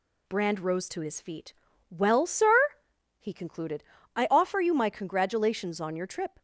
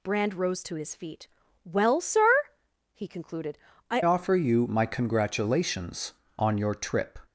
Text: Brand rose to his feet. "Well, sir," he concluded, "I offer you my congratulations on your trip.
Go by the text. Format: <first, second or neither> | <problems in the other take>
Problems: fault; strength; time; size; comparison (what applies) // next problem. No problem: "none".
first | changes voice at "offer"; from 4.0 s on; 3.1 s long